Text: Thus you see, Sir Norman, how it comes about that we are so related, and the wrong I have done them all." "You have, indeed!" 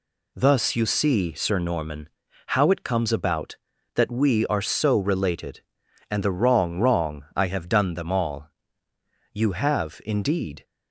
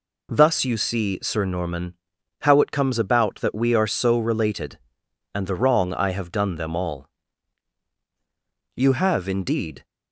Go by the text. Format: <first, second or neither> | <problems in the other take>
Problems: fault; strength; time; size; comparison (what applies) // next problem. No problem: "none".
second | says "wrong" twice; at 6.7 s